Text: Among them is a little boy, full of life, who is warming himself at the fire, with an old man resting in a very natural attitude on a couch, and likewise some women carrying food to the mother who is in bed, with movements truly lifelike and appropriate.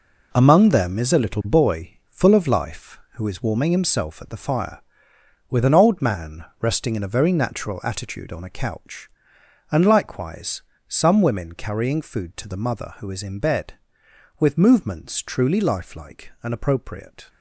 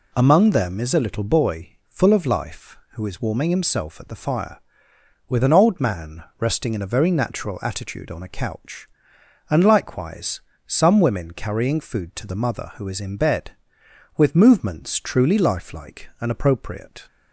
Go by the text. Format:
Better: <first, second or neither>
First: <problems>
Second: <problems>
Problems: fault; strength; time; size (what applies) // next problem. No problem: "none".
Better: second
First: gets quieter; strong; throughout; 9.5 dB // pauses between "man" and "resting"; slight; at 6.4 s; 0.16 s long // pauses between "likewise" and "some"; slight; at 10.6 s; 0.24 s long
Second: pauses between "man" and "resting"; slight; at 6.2 s; 0.16 s long // pauses between "likewise" and "some"; slight; at 10.4 s; 0.24 s long